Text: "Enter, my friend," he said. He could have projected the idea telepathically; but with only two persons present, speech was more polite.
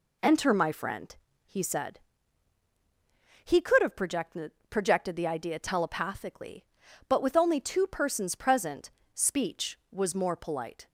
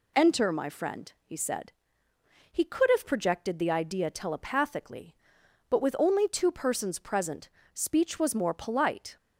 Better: second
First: says "projected" twice; at 4.6 s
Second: none

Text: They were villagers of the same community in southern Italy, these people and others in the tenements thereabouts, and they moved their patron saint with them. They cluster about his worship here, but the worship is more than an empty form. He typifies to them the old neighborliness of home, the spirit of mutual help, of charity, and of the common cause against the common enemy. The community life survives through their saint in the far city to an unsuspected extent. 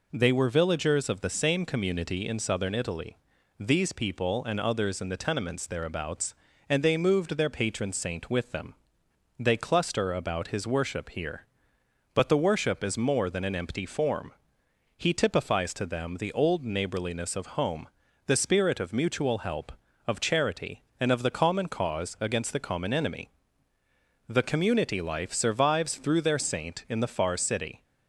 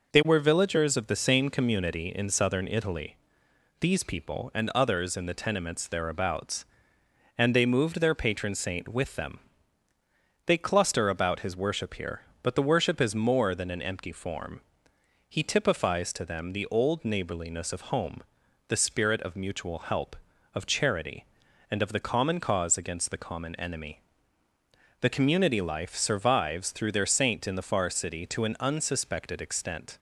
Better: second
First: stops before "to an unsuspected extent"; at 27.8 s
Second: none

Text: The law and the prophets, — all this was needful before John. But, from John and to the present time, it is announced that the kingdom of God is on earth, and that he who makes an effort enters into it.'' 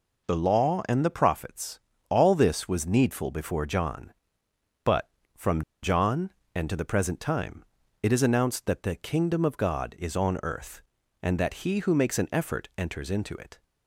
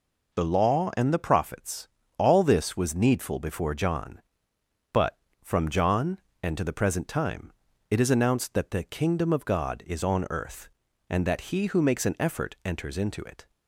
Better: second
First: pauses between "from" and "John"; slight; at 5.6 s; 0.20 s long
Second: none

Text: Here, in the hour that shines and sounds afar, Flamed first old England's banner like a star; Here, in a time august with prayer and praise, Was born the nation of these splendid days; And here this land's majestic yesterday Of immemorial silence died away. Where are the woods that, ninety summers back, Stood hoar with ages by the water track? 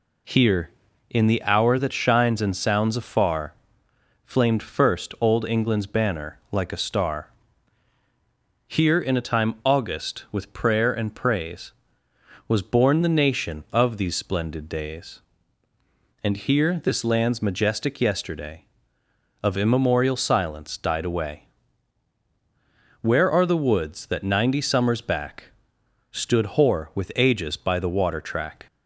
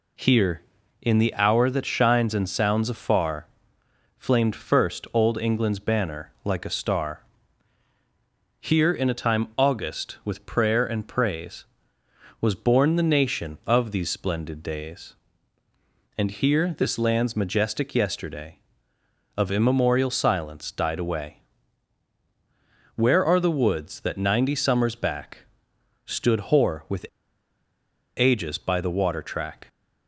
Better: first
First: none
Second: pauses between "with" and "ages"; at 27.0 s; 1.1 s long

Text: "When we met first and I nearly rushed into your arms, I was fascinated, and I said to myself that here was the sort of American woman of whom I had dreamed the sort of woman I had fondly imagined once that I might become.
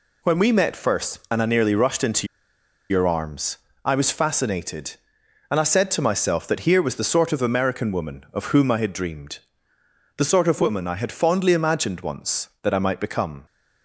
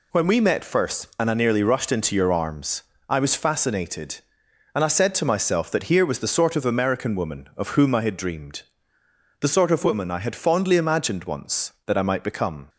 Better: second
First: pauses between "into" and "your"; noticeable; at 2.2 s; 0.64 s long // pauses between "dreamed" and "the"; noticeable; at 9.3 s; 0.78 s long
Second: pauses between "dreamed" and "the"; noticeable; at 8.6 s; 0.78 s long

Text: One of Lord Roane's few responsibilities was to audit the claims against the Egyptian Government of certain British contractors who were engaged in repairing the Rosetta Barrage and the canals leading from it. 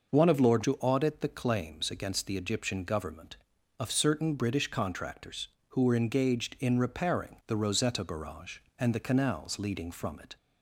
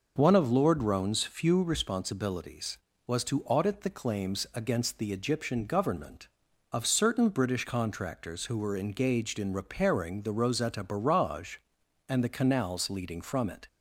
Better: second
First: skips "Roane's few responsibilities was"; at 0.6 s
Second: none

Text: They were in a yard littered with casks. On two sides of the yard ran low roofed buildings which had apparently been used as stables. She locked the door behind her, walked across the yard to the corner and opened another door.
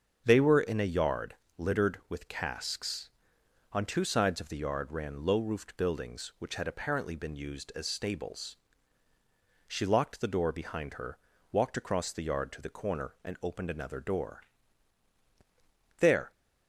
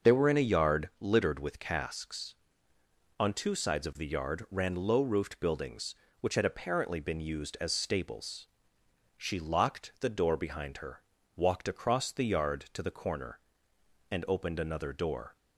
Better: second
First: starts louder than the rest; strong; until 1.2 s; 7.5 dB // pauses between "yard" and "littered"; slight; at 1.3 s; 0.24 s long // goes on to say "There"; slight; from 15.9 s on; 0.34 s long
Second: starts louder than the rest; noticeable; until 1.1 s; 6 dB

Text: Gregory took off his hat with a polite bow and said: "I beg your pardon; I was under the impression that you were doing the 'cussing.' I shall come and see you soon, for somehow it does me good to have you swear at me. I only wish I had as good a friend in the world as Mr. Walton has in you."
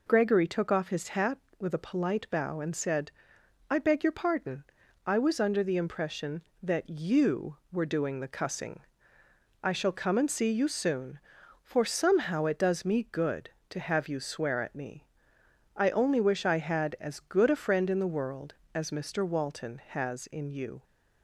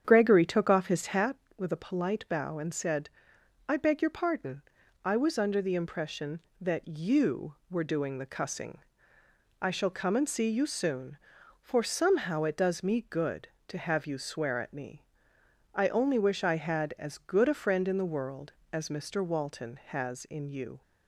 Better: first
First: none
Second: starts louder than the rest; strong; until 1.3 s; 8.5 dB

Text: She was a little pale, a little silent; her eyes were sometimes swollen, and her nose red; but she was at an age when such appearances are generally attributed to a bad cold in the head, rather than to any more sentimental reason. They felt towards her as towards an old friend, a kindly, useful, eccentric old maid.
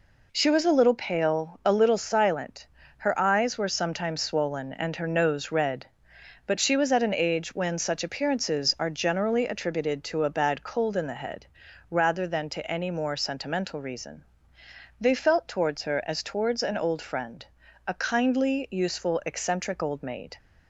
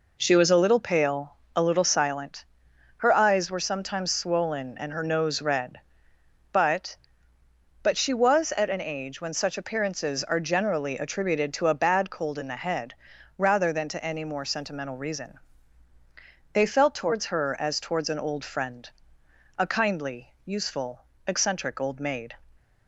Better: first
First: none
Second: says "but" twice; at 7.8 s

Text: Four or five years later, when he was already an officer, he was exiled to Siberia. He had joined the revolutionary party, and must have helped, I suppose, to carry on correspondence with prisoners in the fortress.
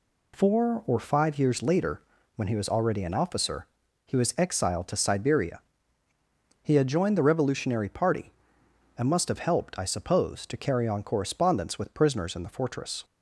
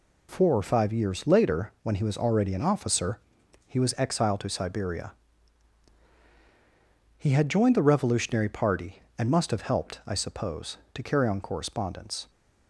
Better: first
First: none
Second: stops before "with prisoners in the fortress"; at 12.2 s

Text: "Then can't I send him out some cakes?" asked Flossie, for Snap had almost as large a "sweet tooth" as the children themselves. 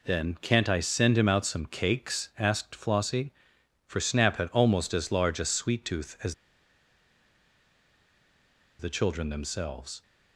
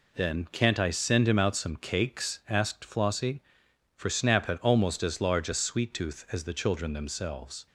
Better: second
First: pauses between "as" and "the"; strong; at 6.3 s; 2.4 s long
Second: none

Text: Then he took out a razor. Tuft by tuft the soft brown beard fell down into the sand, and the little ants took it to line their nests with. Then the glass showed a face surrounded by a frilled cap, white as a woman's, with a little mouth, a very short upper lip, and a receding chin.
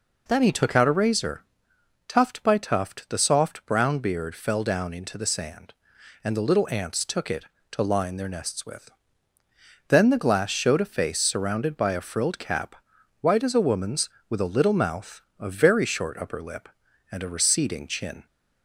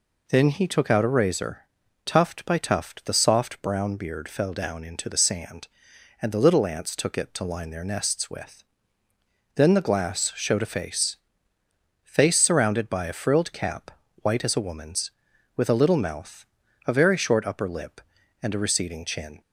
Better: first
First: none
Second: says "face" twice; at 12.0 s

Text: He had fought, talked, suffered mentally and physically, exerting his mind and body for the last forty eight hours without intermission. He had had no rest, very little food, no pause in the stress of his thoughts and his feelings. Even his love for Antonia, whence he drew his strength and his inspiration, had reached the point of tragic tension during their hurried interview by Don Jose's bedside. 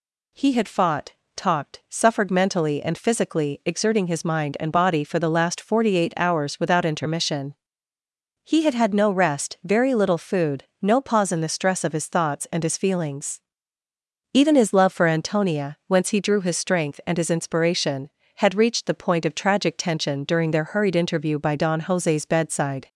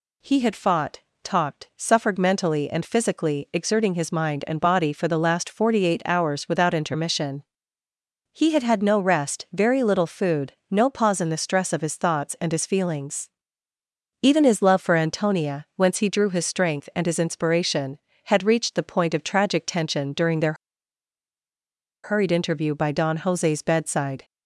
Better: first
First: none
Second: pauses between "their" and "hurried"; strong; at 20.5 s; 1.5 s long

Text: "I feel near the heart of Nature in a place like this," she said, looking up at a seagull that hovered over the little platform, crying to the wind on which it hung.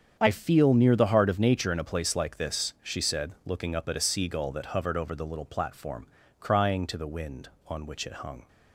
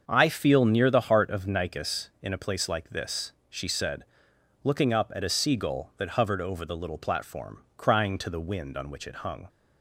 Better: first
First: starts louder than the rest; strong; until 1.2 s; 8 dB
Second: starts louder than the rest; until 1.0 s; 6.5 dB // says "Nicus" for "Nature"; at 1.4 s

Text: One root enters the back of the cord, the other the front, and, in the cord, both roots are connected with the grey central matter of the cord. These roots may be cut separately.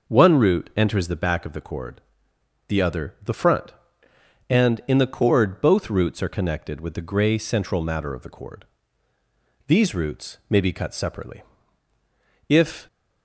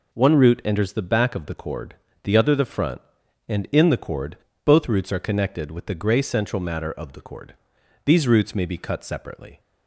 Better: second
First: goes on to say "If"; slight; from 12.4 s on; 0.38 s long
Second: none

